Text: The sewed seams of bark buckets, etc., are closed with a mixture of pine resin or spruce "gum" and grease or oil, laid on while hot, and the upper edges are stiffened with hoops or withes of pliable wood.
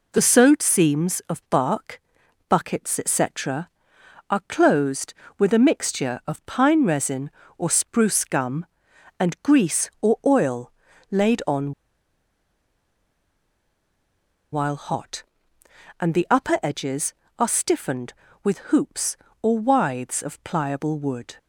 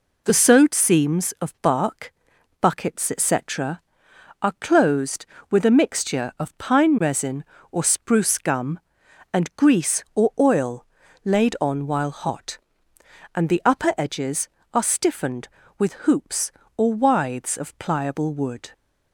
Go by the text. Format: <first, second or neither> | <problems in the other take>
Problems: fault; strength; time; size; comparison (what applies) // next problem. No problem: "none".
second | pauses between "bark" and "buckets"; noticeable; at 2.0 s; 0.48 s long; noticeable in the second // pauses between "on" and "while"; strong; at 11.7 s; 2.8 s long // pauses between "with" and "hoops"; slight; at 18.5 s; 0.16 s long; slight in the second